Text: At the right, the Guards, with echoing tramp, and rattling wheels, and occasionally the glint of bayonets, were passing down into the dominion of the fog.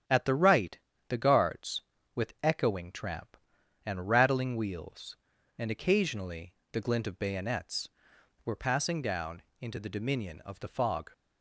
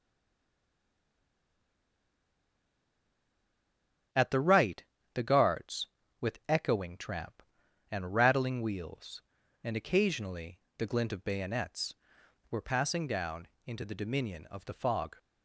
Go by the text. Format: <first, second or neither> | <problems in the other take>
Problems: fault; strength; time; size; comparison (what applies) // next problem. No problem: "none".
first | stays silent before the first word; strong; until 4.1 s; 4.1 s long // starts louder than the rest; strong; until 5.4 s; 10 dB; strong in the first // pauses between "occasionally" and "the"; slight; at 10.5 s; 0.20 s long; slight in the first // pauses between "down" and "into"; slight; at 13.4 s; 0.18 s long; slight in the first